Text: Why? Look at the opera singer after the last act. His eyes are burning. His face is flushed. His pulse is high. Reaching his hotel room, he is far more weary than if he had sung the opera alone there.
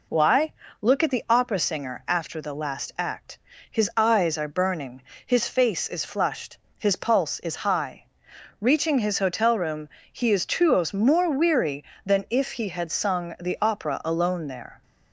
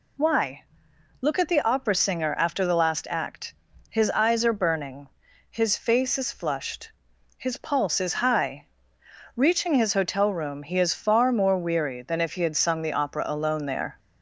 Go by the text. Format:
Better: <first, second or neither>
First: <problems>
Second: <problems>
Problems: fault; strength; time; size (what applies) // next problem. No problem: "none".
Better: second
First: says "tuos" for "far"; at 10.4 s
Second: none